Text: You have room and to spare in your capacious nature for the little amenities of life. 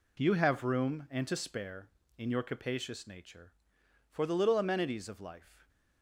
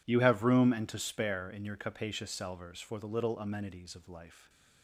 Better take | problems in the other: first | says "salvers" for "nature"; at 2.2 s // stays silent after the last word; slight; from 4.2 s on; 0.6 s long

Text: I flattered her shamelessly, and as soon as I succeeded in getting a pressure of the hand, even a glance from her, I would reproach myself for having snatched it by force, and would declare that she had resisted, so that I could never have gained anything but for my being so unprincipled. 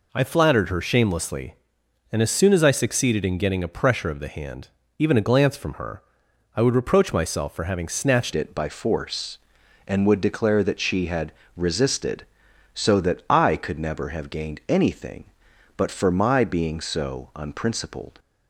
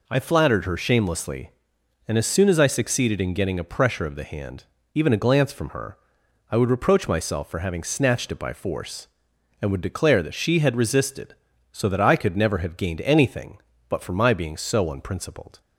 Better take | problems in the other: second | changes voice at "it"; from 8.3 s on; 9.8 s long // pauses between "had" and "resisted"; slight; at 11.3 s; 0.24 s long

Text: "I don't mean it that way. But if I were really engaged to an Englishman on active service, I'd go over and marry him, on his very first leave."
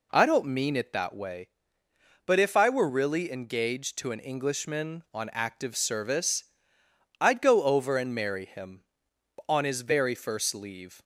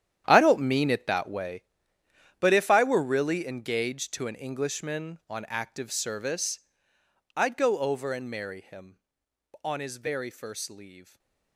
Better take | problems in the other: first | gets quieter; strong; throughout; 15.5 dB // stays silent after the last word; slight; from 11.0 s on; 0.5 s long

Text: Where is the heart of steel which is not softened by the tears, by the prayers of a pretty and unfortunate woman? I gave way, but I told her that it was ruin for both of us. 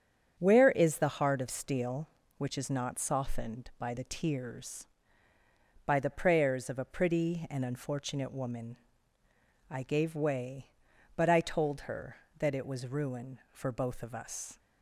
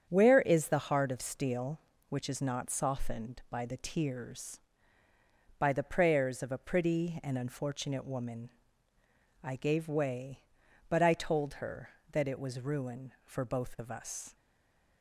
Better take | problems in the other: first | starts louder than the rest; strong; until 1.1 s; 8 dB; strong in the first // stays silent after the last word; slight; from 14.3 s on; 0.7 s long

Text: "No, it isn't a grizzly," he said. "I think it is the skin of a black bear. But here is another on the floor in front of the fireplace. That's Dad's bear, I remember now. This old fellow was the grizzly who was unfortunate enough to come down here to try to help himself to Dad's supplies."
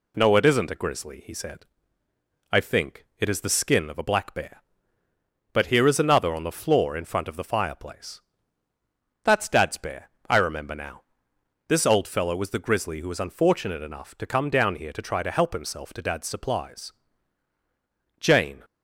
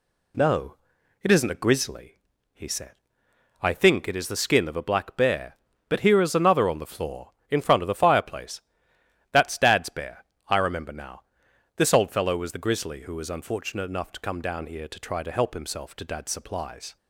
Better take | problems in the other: second | goes on to say "Jane"; slight; from 18.2 s on; 0.44 s long

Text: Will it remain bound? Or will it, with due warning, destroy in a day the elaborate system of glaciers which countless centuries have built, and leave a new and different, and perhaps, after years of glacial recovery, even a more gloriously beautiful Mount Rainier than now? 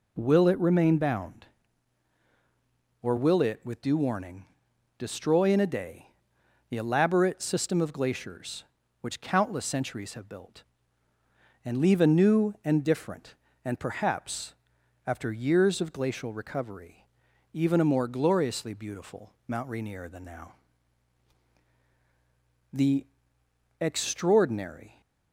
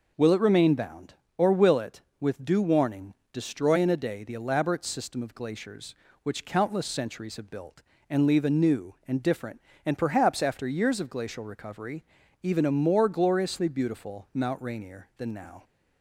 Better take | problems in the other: second | pauses between "day" and "the"; noticeable; at 6.0 s; 0.62 s long // goes on to say "The extraordinary"; strong; from 22.7 s on; 2.2 s long

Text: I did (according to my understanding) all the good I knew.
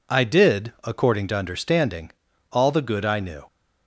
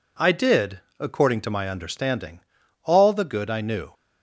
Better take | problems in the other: second | skips "my"; at 1.3 s

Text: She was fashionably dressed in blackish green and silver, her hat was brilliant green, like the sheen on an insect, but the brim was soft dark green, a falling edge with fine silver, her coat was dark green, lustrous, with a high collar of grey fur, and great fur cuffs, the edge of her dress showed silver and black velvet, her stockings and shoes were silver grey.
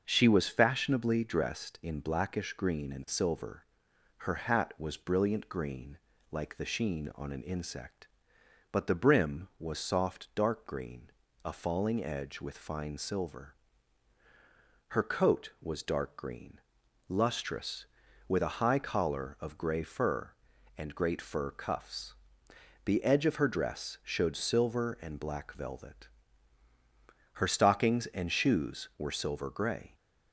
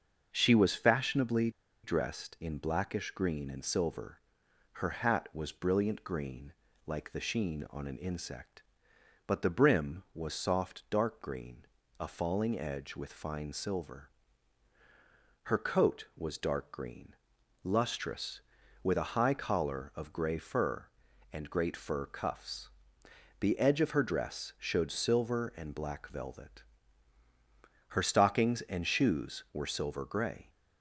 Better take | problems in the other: first | starts louder than the rest; until 1.3 s; 6.5 dB; also in the first // pauses between "fashionably" and "dressed"; slight; at 1.4 s; 0.34 s long

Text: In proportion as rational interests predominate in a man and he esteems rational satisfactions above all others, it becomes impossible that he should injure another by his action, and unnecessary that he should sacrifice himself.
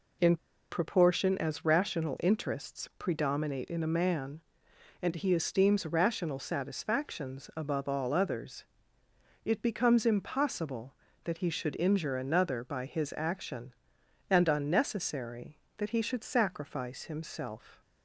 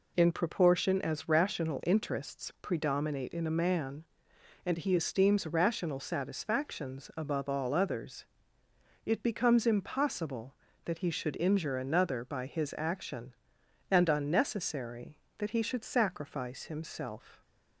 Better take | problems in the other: second | pauses between "In" and "proportion"; slight; at 0.3 s; 0.34 s long

